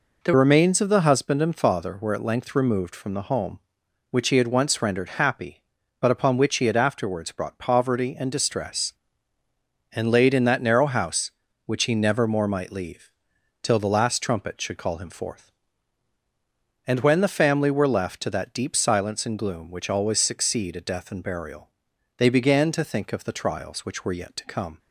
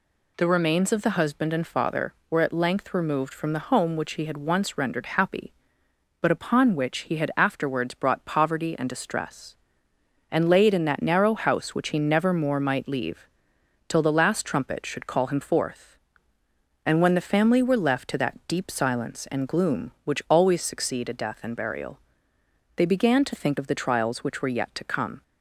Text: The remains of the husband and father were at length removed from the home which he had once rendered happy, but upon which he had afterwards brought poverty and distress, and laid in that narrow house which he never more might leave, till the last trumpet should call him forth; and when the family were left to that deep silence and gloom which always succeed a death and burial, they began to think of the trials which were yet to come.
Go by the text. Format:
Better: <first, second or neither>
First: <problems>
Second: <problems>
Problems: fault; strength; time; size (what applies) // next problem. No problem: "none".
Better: second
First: changes voice at "remains"; from 0.3 s on; 24.4 s long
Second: none